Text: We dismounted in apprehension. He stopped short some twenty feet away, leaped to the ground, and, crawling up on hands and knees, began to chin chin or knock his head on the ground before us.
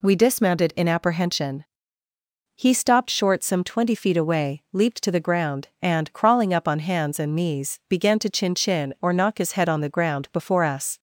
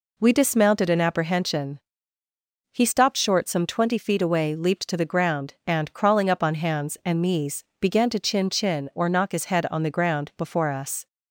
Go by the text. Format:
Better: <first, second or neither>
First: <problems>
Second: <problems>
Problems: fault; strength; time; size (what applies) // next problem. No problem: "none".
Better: neither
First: none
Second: none